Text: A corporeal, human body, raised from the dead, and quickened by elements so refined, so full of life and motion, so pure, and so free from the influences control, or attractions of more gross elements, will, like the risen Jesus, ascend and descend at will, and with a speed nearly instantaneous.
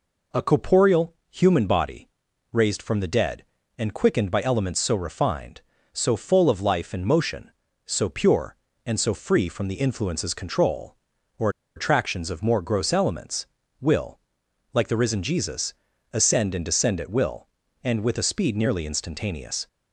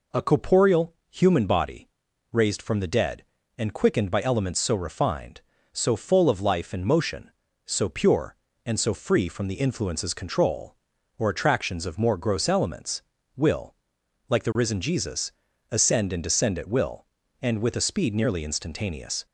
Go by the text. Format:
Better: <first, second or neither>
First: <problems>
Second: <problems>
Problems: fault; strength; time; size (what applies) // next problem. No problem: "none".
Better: second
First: pauses between "or" and "attractions"; slight; at 11.4 s; 0.27 s long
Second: none